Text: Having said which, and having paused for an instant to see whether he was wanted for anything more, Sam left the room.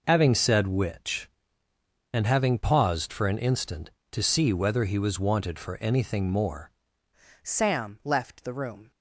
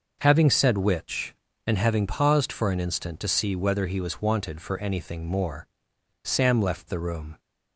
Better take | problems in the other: second | changes voice at "Sam"; from 7.4 s on; 1.5 s long

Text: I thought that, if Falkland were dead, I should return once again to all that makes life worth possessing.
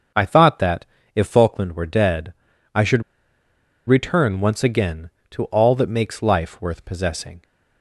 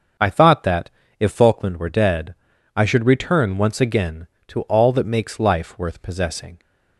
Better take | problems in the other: second | starts louder than the rest; until 1.4 s; 7 dB; also in the second // pauses between "should" and "return"; noticeable; at 3.0 s; 0.86 s long

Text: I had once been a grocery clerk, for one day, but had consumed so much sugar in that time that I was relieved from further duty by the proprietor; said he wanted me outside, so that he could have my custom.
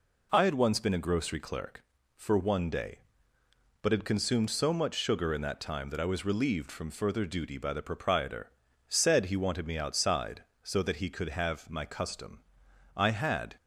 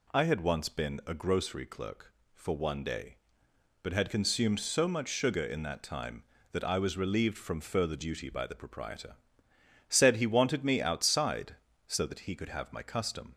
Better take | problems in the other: second | goes on to say "I had"; from 12.9 s on; 0.60 s long

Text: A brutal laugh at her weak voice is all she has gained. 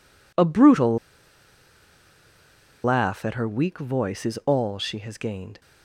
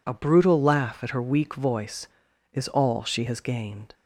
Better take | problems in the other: second | pauses between "brutal" and "laugh"; strong; at 0.9 s; 1.8 s long

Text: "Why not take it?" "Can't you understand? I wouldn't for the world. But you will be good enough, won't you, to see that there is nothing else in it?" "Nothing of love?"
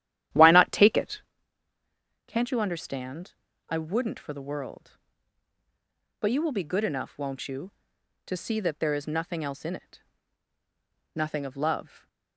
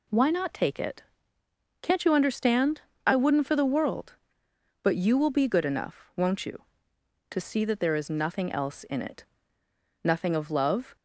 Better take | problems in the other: second | starts louder than the rest; strong; until 1.3 s; 12 dB

